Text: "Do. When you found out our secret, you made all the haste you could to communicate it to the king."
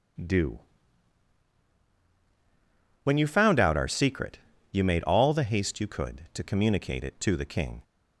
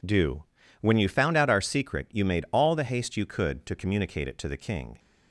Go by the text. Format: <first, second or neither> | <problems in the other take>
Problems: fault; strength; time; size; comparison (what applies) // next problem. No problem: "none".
neither | none